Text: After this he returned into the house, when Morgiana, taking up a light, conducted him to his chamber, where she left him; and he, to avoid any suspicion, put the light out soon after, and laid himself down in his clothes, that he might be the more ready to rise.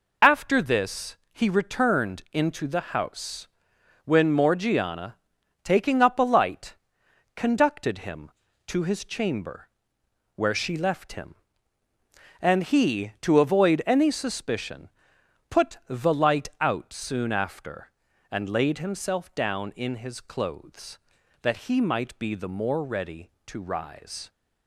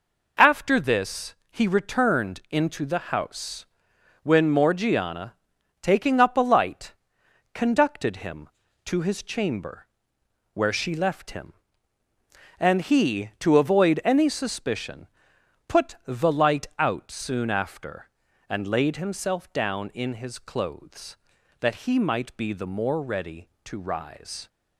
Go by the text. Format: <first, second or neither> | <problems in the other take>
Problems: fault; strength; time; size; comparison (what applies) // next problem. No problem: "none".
second | loses the start of "After"; at 0.2 s; 35 ms // pauses between "this" and "he"; slight; at 1.1 s; 0.16 s long; slight in the second